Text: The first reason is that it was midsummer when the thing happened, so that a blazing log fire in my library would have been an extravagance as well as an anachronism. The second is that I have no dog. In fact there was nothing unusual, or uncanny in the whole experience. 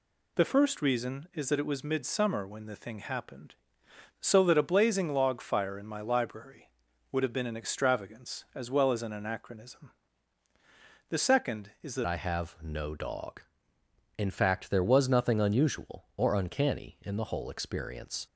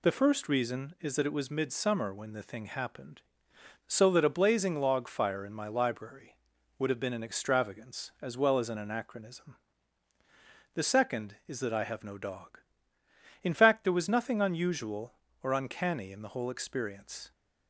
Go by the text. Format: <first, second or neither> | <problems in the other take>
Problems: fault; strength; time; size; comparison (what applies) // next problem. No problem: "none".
second | changes voice at "I"; from 12.0 s on; 6.2 s long